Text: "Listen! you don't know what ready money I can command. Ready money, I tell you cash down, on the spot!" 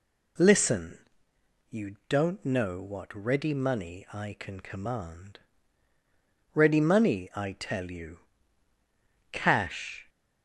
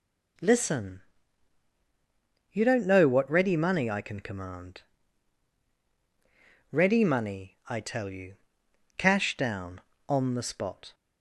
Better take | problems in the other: second | pauses between "you" and "cash"; at 8.1 s; 1.1 s long; noticeable in the second // stops before "down on the spot"; at 10.0 s

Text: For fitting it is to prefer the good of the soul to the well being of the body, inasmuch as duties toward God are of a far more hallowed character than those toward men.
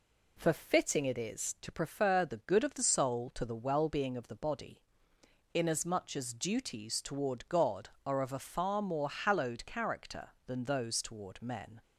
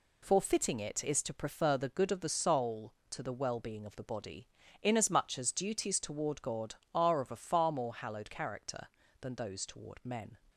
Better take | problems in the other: neither | none

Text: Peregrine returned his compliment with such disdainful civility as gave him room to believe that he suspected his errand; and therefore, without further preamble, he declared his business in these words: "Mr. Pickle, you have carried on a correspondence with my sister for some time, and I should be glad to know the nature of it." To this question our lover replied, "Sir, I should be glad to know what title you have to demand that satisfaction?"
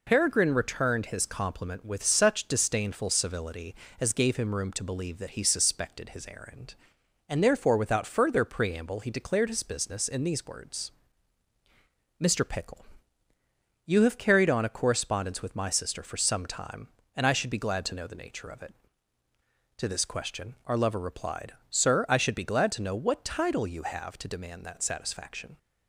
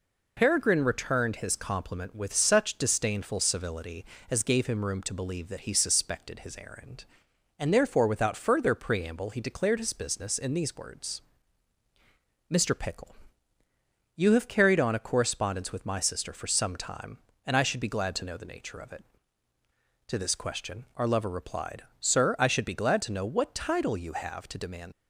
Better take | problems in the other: first | stops before "that satisfaction"; at 24.9 s

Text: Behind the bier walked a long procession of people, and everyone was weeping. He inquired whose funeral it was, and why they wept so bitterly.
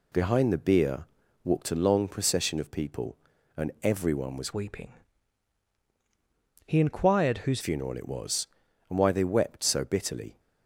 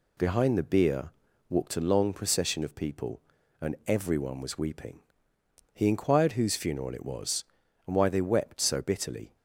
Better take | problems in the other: second | pauses between "bier" and "walked"; slight; at 1.0 s; 0.36 s long; slight in the second // changes voice from "weeping" to "whose"; from 4.5 to 7.6 s; 3.1 s long

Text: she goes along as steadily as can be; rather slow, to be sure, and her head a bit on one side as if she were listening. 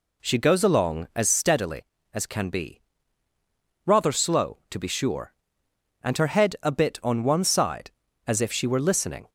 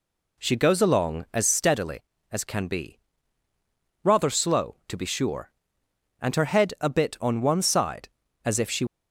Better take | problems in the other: first | stops before "were listening"; at 8.8 s

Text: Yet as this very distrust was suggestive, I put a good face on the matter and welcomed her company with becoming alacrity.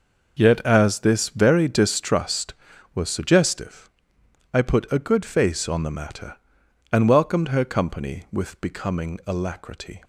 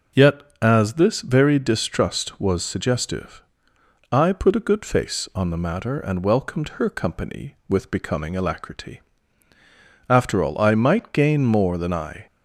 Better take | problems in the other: first | goes on to say "After all I might gain more than I"; strong; from 10.0 s on; 2.1 s long

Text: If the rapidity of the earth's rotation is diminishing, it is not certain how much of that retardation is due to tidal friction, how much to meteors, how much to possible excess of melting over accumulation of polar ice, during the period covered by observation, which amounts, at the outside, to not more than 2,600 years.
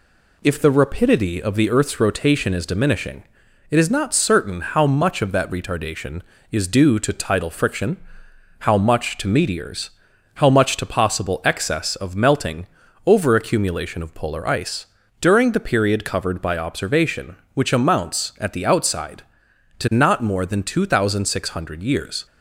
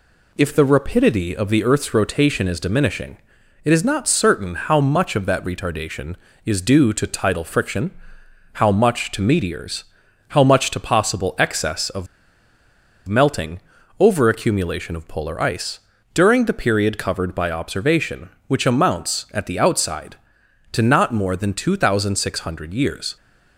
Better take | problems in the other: first | pauses between "of" and "melting"; at 12.0 s; 1.0 s long // pauses between "melting" and "over"; at 13.5 s; 0.38 s long; also in the first

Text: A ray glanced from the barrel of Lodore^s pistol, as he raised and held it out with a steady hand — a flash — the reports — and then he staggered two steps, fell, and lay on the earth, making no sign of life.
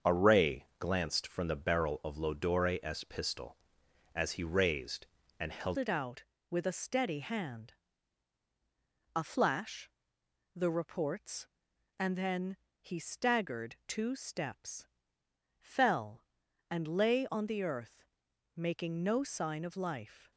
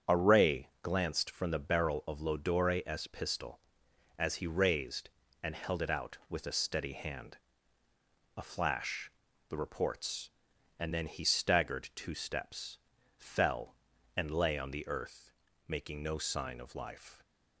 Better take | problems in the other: second | starts louder than the rest; until 1.2 s; 7 dB; strong in the second // pauses between "ray" and "glanced"; slight; at 0.6 s; 0.16 s long; slight in the second // changes voice at "it"; from 5.7 s on; 14.6 s long // pauses between "then" and "he"; slight; at 12.5 s; 0.26 s long

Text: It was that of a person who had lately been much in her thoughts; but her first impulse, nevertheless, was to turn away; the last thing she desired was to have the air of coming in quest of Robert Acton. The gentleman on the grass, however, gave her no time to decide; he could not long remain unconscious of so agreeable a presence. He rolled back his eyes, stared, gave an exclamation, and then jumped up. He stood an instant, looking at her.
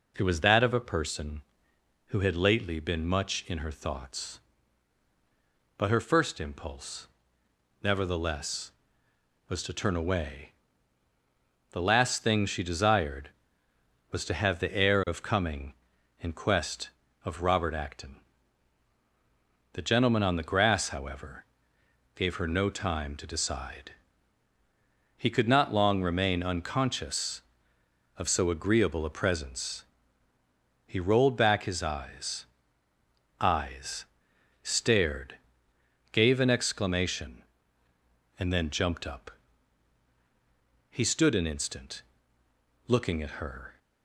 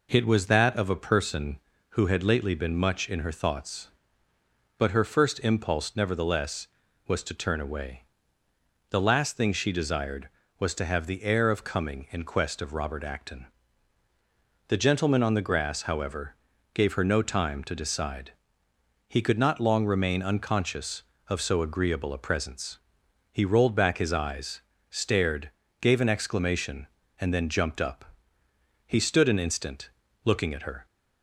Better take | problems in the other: second | says "eyes" twice; at 33.3 s

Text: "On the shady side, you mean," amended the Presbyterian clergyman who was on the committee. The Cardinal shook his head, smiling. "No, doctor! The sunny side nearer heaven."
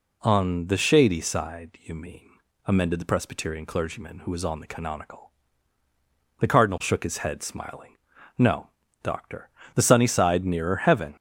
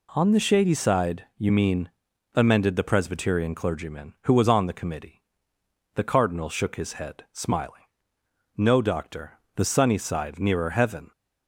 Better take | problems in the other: second | says "canonical" for "committee"; at 4.6 s

